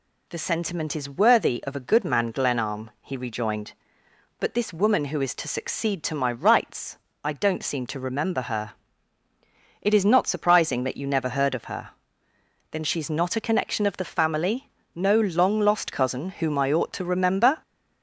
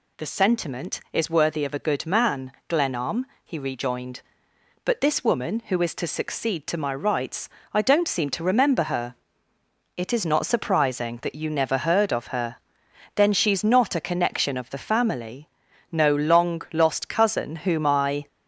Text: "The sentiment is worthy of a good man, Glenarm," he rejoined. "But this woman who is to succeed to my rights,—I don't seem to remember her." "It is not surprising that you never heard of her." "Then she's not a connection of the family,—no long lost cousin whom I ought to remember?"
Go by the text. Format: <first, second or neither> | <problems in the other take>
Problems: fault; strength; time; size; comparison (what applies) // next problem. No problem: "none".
first | stops before "ought to remember"; at 18.2 s